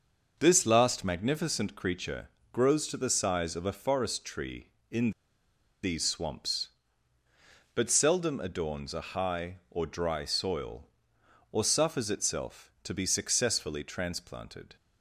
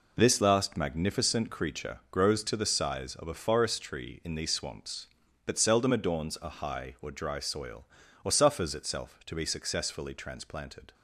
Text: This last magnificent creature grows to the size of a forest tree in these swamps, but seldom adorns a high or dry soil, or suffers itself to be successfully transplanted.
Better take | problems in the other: second | starts louder than the rest; until 1.4 s; 6 dB // pauses between "creature" and "grows"; slight; at 2.2 s; 0.24 s long // pauses between "in" and "these"; noticeable; at 5.1 s; 0.71 s long

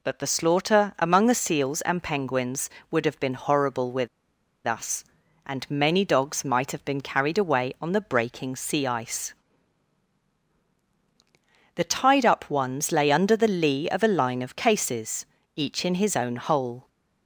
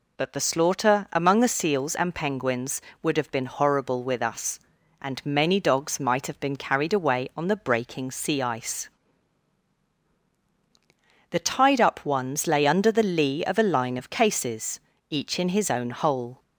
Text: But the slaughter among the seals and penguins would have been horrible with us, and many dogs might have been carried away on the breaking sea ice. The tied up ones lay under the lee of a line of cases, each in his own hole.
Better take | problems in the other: second | pauses between "with" and "us"; noticeable; at 4.0 s; 0.57 s long

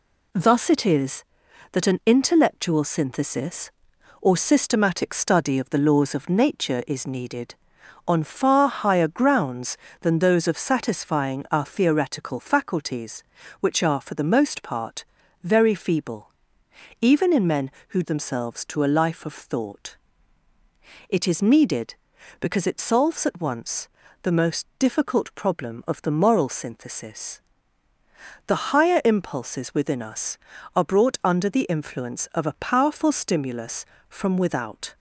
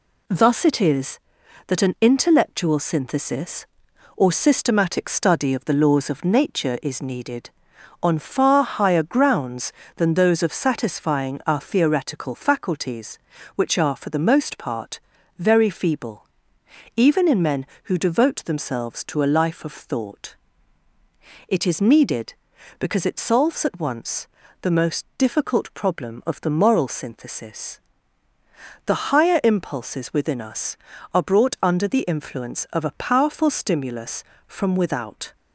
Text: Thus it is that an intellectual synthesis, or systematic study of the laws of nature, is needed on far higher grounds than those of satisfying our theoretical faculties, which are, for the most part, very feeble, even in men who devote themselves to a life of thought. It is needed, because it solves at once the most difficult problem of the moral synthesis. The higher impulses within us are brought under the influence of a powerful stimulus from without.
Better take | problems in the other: second | skips "devote"; at 18.0 s // pauses between "once" and "the"; slight; at 23.8 s; 0.36 s long; slight in the second

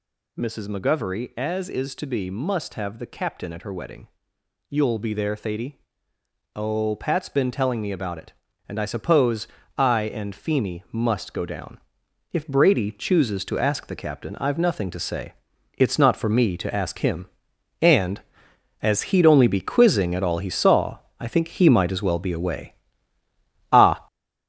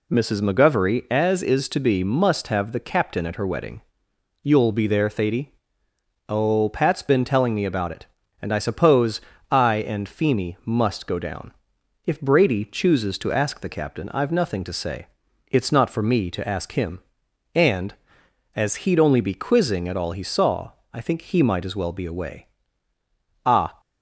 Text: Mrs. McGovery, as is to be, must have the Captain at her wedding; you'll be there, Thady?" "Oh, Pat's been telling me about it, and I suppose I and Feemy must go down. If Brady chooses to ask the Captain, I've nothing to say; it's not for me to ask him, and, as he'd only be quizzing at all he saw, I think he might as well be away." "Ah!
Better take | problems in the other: second | gets louder; throughout; 6.5 dB // pauses between "suppose" and "I"; slight; at 9.4 s; 0.32 s long; slight in the second

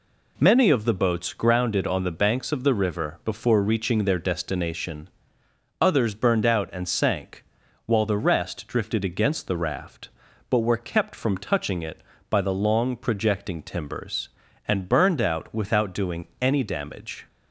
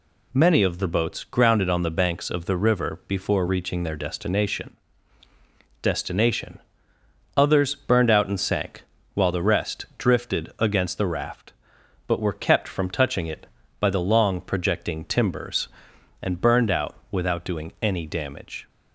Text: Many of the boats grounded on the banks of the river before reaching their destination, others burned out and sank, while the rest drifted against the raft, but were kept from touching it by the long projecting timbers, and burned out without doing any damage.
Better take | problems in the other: first | says "destination" twice; at 5.8 s // pauses between "out" and "without"; slight; at 16.9 s; 0.16 s long

